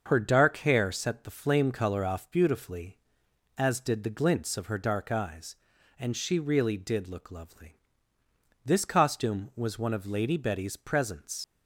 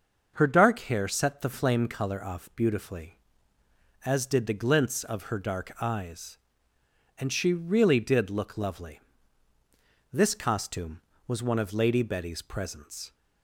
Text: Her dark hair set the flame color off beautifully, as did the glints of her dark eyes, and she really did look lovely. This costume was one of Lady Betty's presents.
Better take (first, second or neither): second